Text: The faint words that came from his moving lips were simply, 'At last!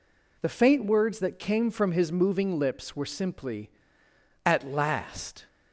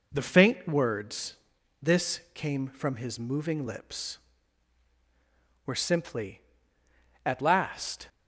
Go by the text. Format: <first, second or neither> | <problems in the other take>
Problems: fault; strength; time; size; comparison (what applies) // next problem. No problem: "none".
first | says "this" for "that"; at 1.8 s